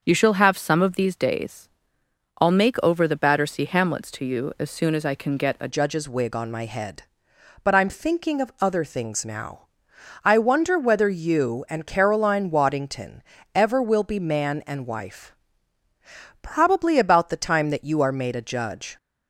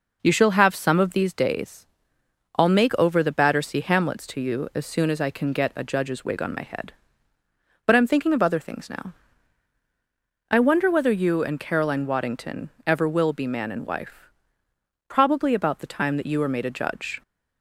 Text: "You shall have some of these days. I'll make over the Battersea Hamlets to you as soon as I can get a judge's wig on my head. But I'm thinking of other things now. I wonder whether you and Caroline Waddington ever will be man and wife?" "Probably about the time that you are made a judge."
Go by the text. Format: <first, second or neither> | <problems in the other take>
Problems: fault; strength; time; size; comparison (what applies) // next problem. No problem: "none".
second | starts louder than the rest; until 1.0 s; 6.5 dB // changes voice at "judge's"; from 5.6 s on; 13.3 s long // pauses between "Waddington" and "ever"; slight; at 13.2 s; 0.34 s long; slight in the second